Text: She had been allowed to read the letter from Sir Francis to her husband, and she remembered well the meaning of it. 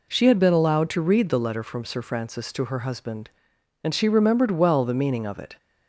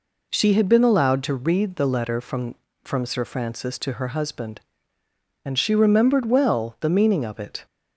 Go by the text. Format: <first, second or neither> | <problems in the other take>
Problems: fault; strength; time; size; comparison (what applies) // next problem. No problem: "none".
first | says "from" twice; at 2.8 s